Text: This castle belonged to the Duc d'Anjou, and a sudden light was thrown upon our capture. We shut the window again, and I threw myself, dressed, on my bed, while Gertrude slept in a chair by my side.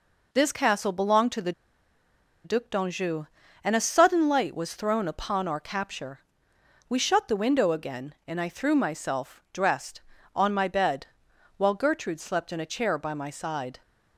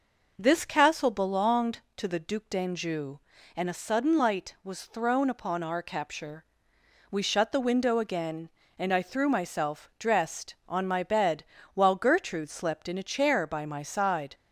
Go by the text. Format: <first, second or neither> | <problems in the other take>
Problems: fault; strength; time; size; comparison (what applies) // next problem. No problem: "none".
second | pauses between "the" and "Duc"; noticeable; at 1.5 s; 0.93 s long